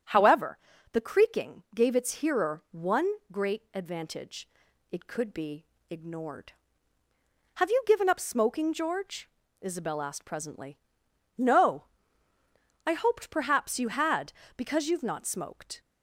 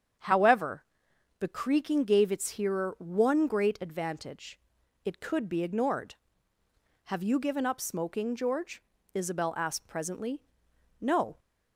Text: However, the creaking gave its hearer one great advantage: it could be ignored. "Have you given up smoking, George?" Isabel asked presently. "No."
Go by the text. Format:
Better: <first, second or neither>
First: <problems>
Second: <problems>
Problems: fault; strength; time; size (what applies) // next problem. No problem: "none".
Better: second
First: starts louder than the rest; until 1.4 s; 6.5 dB // pauses between "one" and "great"; slight; at 3.0 s; 0.24 s long // pauses between "be" and "ignored"; slight; at 5.6 s; 0.26 s long // goes on to say "I hoped perhaps you had because you've not smoked"; strong; from 12.8 s on; 2.9 s long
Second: starts louder than the rest; strong; until 1.7 s; 8 dB